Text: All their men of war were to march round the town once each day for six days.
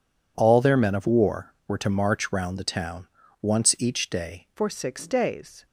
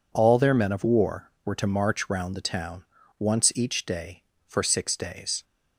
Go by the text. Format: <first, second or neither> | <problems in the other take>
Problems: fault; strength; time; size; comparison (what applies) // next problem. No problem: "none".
second | pauses between "town" and "once"; slight; at 3.0 s; 0.32 s long; slight in the second // changes voice at "for"; from 4.5 s on; 1.1 s long